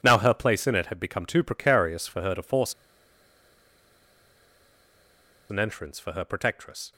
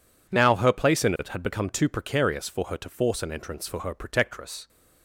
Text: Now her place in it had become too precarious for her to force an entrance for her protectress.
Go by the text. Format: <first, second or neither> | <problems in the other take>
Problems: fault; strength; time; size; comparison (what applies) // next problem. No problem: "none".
second | pauses between "force" and "an"; strong; at 2.7 s; 2.7 s long